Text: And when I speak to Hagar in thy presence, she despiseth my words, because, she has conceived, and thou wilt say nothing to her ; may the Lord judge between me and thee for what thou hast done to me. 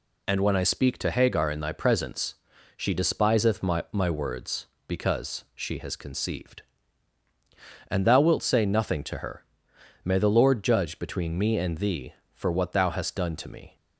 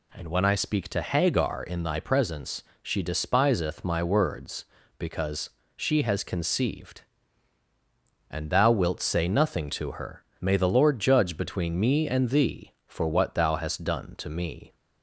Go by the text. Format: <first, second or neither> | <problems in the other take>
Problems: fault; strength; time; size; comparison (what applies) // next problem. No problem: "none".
second | says "my" twice; at 3.9 s